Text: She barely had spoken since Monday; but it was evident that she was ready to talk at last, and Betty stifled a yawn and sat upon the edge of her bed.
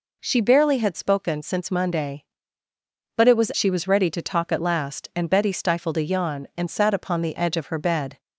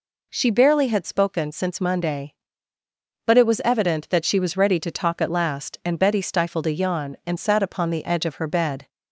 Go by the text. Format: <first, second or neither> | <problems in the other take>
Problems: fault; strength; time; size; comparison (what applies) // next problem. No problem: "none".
second | skips "evident that"; at 3.5 s